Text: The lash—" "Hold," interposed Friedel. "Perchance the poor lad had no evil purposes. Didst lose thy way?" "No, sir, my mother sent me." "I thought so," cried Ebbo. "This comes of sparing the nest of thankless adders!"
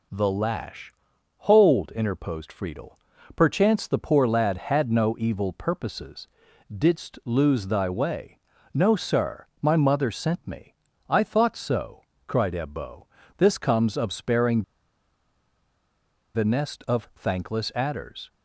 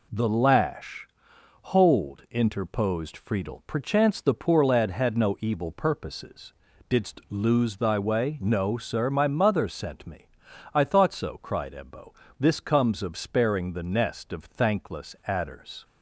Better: second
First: pauses between "sparing" and "the"; strong; at 14.6 s; 1.7 s long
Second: none

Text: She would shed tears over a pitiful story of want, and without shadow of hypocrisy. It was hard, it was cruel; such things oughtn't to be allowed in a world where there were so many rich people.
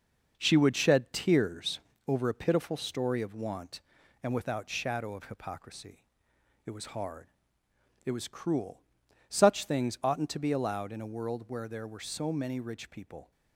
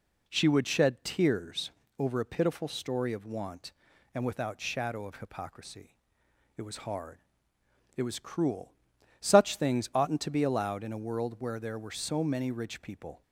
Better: second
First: gets quieter; noticeable; throughout; 6 dB // pauses between "tears" and "over"; slight; at 1.7 s; 0.28 s long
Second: pauses between "tears" and "over"; slight; at 1.6 s; 0.28 s long

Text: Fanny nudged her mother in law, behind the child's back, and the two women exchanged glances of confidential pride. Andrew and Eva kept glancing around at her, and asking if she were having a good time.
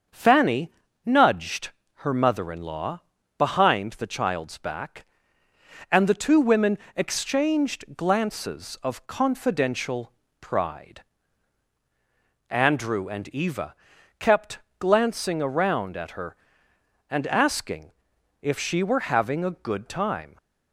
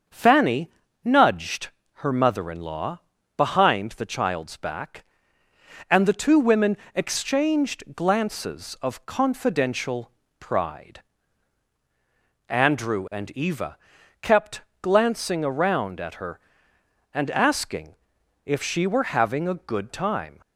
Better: neither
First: starts louder than the rest; until 1.4 s; 7 dB // pauses between "Fanny" and "nudged"; slight; at 0.7 s; 0.34 s long // pauses between "nudged" and "her"; slight; at 1.7 s; 0.26 s long // pauses between "women" and "exchanged"; slight; at 6.7 s; 0.20 s long // pauses between "confidential" and "pride"; slight; at 10.1 s; 0.28 s long // pauses between "Eva" and "kept"; at 13.7 s; 0.44 s long // pauses between "kept" and "glancing"; slight; at 14.5 s; 0.20 s long // pauses between "asking" and "if"; noticeable; at 17.9 s; 0.50 s long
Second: starts louder than the rest; until 1.4 s; 6.5 dB // pauses between "Fanny" and "nudged"; slight; at 0.6 s; 0.34 s long // pauses between "nudged" and "her"; slight; at 1.6 s; 0.26 s long // pauses between "women" and "exchanged"; slight; at 6.7 s; 0.20 s long // pauses between "confidential" and "pride"; slight; at 10.1 s; 0.28 s long // pauses between "Eva" and "kept"; at 13.7 s; 0.44 s long // pauses between "kept" and "glancing"; slight; at 14.6 s; 0.20 s long // pauses between "asking" and "if"; noticeable; at 17.9 s; 0.50 s long

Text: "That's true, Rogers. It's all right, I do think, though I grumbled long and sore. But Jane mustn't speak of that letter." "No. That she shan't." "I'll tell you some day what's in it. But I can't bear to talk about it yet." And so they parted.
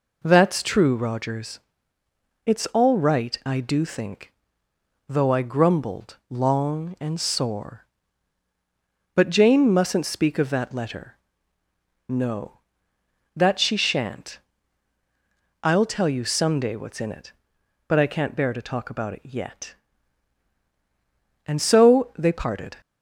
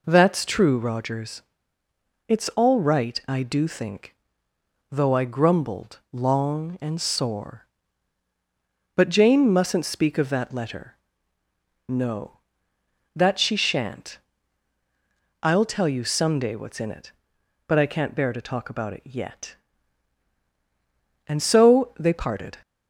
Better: neither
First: none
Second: none

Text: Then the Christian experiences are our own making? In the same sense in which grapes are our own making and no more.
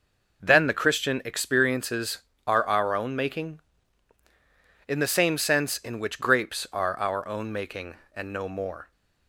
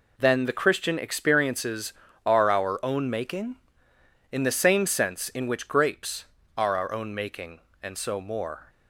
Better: first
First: none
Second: says "so" for "no"; at 7.9 s

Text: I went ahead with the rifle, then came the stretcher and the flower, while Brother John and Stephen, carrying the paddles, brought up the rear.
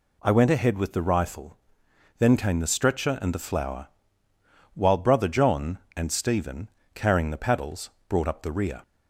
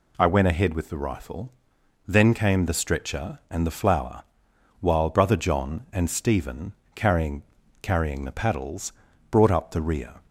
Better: first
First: none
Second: says "carrying" twice; at 7.8 s

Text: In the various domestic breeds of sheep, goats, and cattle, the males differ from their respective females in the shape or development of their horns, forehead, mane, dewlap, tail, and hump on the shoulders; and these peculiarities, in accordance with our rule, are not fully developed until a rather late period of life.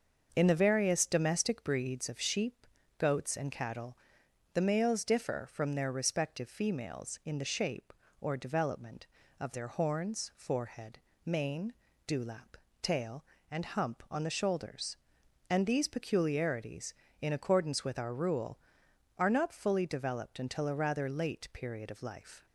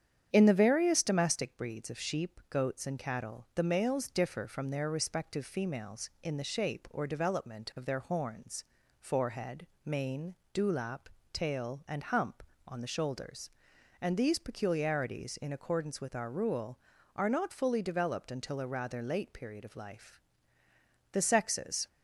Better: first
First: starts louder than the rest; until 1.3 s; 6 dB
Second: starts louder than the rest; strong; until 1.3 s; 9 dB // goes on to say "The sexes"; noticeable; from 21.1 s on; 0.74 s long

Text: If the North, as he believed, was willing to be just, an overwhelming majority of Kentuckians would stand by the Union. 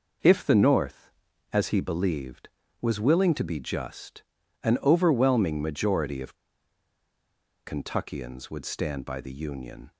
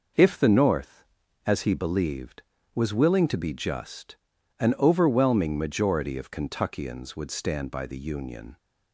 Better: second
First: pauses between "of" and "Kentuckians"; strong; at 6.3 s; 1.3 s long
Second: none

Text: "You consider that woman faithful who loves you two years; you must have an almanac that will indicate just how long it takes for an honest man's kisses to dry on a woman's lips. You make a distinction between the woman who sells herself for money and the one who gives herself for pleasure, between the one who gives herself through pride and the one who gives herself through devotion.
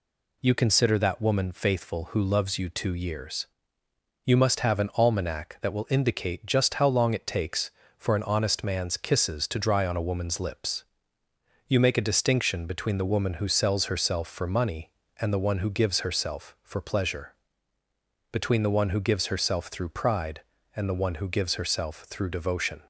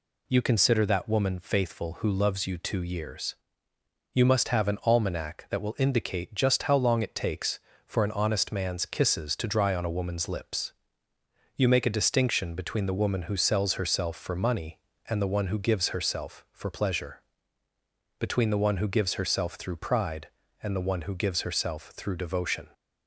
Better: neither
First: none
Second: none

